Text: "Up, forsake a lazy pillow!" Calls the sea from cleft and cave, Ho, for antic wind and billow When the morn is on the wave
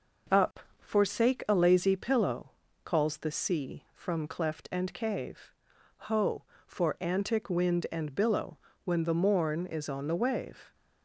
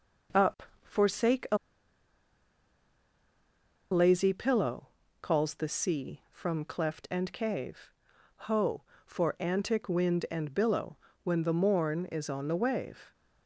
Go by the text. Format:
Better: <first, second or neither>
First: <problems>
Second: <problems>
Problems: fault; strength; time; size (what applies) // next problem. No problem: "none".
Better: first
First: pauses between "billow" and "When"; slight; at 8.5 s; 0.26 s long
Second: pauses between "a" and "lazy"; strong; at 1.5 s; 2.3 s long // pauses between "billow" and "When"; slight; at 10.9 s; 0.26 s long